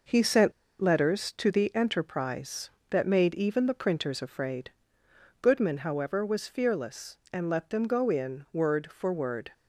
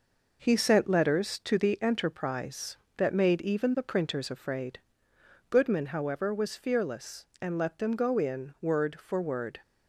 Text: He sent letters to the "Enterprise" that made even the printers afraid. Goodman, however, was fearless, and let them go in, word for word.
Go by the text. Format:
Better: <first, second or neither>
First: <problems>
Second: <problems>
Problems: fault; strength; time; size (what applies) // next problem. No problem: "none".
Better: second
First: pauses between "sent" and "letters"; slight; at 0.5 s; 0.29 s long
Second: none